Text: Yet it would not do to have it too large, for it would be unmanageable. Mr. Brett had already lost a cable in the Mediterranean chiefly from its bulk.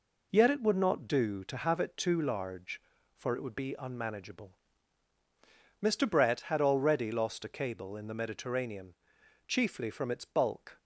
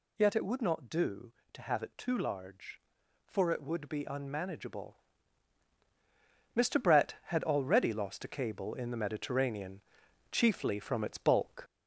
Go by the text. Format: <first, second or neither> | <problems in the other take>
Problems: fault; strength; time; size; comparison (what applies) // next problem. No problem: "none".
first | gets louder; throughout; 4 dB // pauses between "Mediterranean" and "chiefly"; noticeable; at 9.8 s; 0.50 s long; noticeable in the first